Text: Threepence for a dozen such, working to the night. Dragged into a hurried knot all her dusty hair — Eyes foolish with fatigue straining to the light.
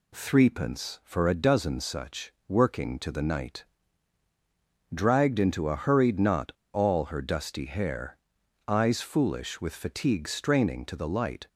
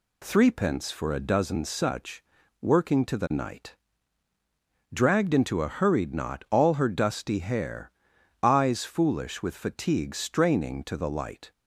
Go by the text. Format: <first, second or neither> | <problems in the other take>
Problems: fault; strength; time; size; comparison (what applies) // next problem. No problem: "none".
second | pauses between "knot" and "all"; slight; at 6.5 s; 0.22 s long